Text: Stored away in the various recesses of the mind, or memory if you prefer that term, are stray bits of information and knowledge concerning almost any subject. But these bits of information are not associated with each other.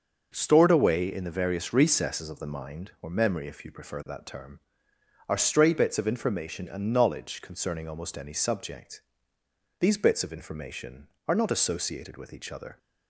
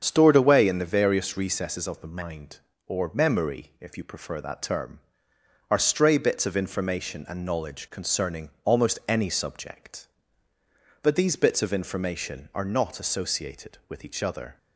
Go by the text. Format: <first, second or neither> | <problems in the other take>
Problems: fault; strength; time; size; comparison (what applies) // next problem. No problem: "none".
second | starts louder than the rest; until 1.3 s; 6.5 dB; strong in the second // skips "But"; at 9.3 s